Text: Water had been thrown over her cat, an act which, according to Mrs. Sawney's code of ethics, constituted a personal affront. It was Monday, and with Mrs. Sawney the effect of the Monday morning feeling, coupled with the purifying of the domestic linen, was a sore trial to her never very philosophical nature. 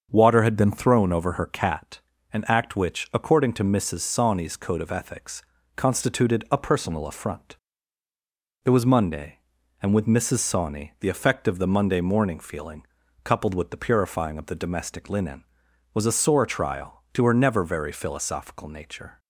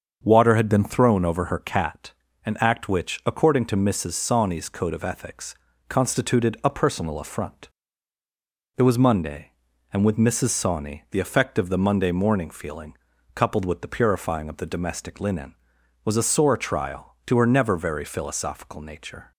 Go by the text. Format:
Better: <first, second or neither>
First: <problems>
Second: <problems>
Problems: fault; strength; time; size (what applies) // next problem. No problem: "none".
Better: neither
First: starts louder than the rest; until 1.1 s; 6.5 dB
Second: starts louder than the rest; until 1.2 s; 6.5 dB